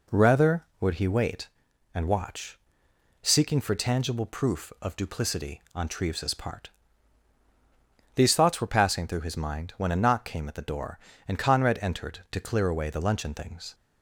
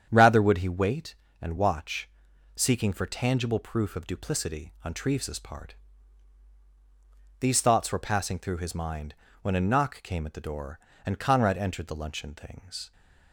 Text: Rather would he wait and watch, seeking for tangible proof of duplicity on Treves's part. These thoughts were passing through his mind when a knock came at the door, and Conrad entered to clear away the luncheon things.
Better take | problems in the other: first | starts louder than the rest; strong; until 1.1 s; 8.5 dB // pauses between "mind" and "when"; slight; at 9.1 s; 0.28 s long // skips "to clear away"; at 11.8 s

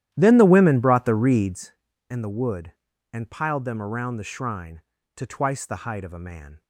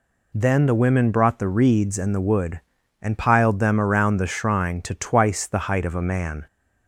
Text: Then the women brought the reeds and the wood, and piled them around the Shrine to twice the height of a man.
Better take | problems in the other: second | starts louder than the rest; strong; until 1.8 s; 12.5 dB

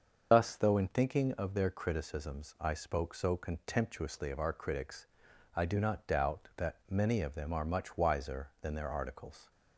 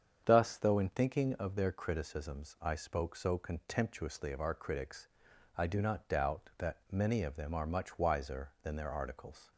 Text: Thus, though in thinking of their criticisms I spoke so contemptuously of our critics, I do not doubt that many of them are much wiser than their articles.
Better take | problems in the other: second | loses the start of "Thus"; at 0.3 s; 75 ms // starts louder than the rest; until 1.3 s; 6 dB; strong in the second

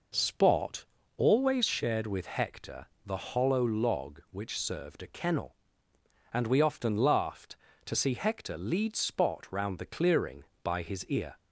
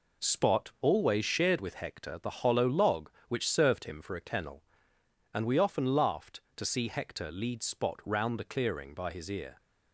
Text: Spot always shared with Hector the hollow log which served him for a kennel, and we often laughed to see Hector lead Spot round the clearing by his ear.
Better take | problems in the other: second | pauses between "Spot" and "always"; slight; at 0.8 s; 0.32 s long // pauses between "Hector" and "the"; slight; at 2.8 s; 0.18 s long // skips "him for"; at 5.0 s

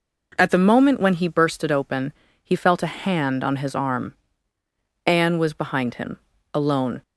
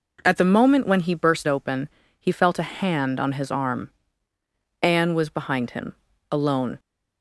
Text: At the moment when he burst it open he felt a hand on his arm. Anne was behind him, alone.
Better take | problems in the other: first | skips "it"; at 1.4 s // pauses between "open" and "he"; slight; at 1.8 s; 0.32 s long; slight in the first

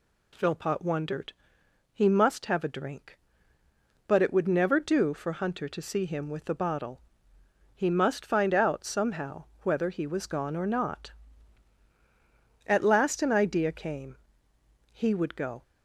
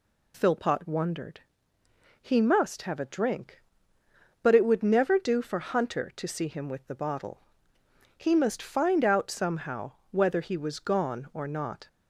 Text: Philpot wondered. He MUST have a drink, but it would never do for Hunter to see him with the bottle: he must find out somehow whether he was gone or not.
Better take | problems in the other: second | pauses between "somehow" and "whether"; slight; at 9.4 s; 0.18 s long; slight in the second // goes on to say "At last an idea came He would go"; strong; from 12.6 s on; 2.9 s long

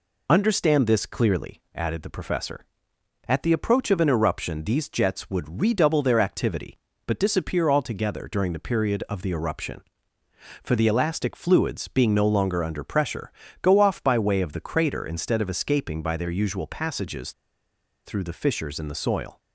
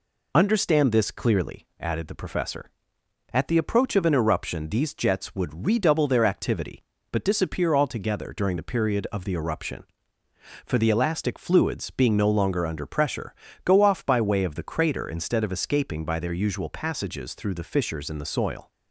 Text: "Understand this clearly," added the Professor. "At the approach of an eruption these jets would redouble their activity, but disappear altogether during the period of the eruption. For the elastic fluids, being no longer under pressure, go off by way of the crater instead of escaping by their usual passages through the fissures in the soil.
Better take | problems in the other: second | pauses between "passages" and "through"; noticeable; at 17.3 s; 0.75 s long

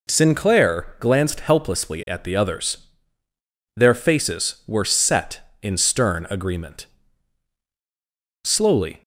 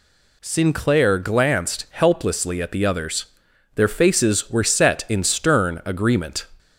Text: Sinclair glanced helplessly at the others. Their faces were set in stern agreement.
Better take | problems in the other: second | goes on to say "Slowly"; from 8.4 s on; 0.58 s long

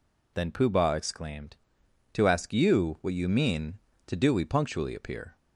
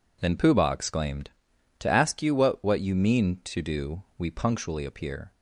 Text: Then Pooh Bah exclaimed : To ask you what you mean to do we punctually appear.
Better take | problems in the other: first | says "what" twice; at 2.6 s

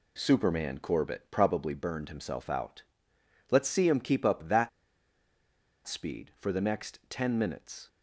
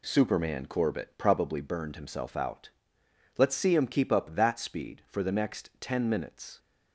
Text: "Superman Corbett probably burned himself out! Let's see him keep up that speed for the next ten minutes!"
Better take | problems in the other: second | pauses between "that" and "speed"; at 4.6 s; 1.1 s long

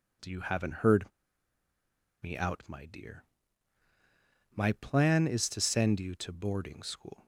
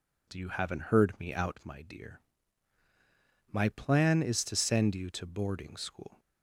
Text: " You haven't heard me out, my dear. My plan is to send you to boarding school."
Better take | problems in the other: second | pauses between "heard" and "me"; at 1.0 s; 1.1 s long

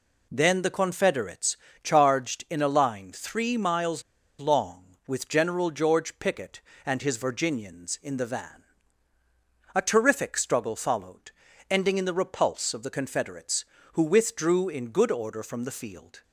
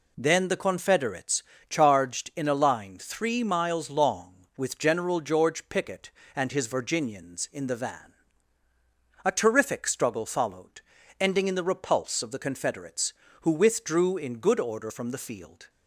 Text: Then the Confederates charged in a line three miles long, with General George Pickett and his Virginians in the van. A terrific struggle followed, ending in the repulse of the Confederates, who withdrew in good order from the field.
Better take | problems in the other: second | pauses between "Confederates" and "charged"; slight; at 1.5 s; 0.26 s long; slight in the second // pauses between "miles" and "long"; at 4.0 s; 0.38 s long

